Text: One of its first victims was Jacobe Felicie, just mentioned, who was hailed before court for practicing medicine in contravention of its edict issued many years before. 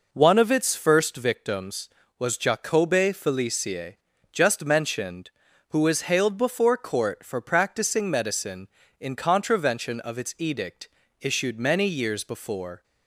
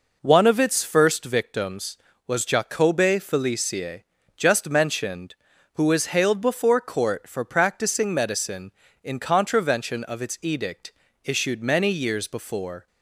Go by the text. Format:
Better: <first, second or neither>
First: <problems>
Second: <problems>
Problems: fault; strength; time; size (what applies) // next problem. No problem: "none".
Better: neither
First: pauses between "edict" and "issued"; slight; at 10.8 s; 0.32 s long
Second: pauses between "edict" and "issued"; slight; at 10.9 s; 0.32 s long